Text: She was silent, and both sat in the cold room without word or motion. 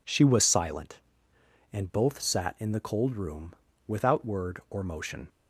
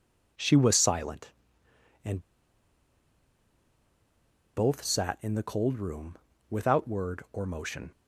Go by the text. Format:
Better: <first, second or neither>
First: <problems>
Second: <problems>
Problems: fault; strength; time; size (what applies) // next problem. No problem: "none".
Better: first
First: pauses between "room" and "without"; slight; at 3.5 s; 0.34 s long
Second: pauses between "and" and "both"; strong; at 2.1 s; 2.3 s long // pauses between "room" and "without"; slight; at 6.1 s; 0.34 s long